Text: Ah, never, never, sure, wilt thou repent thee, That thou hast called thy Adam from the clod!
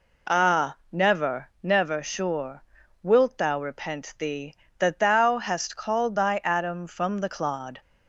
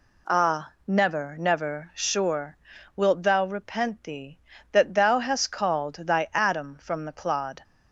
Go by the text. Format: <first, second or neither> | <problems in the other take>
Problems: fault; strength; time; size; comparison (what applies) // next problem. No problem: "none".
neither | none